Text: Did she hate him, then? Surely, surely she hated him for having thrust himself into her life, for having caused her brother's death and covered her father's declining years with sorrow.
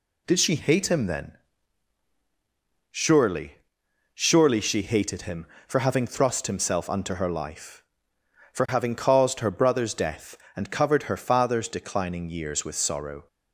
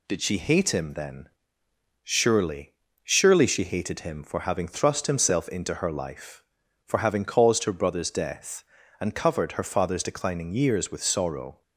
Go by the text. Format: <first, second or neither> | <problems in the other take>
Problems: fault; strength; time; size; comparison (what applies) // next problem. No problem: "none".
second | says "unto" for "into"; at 6.8 s